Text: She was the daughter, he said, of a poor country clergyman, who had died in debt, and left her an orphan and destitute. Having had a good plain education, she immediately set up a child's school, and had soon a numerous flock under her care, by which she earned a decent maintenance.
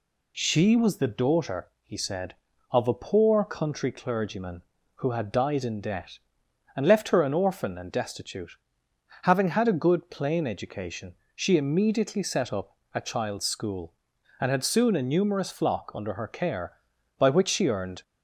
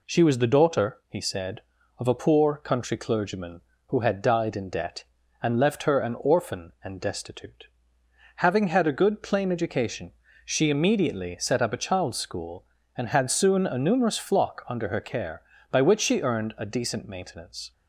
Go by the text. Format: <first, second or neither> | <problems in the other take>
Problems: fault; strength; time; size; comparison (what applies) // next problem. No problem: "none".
second | pauses between "up" and "a"; slight; at 12.7 s; 0.16 s long // stops before "a decent maintenance"; at 18.0 s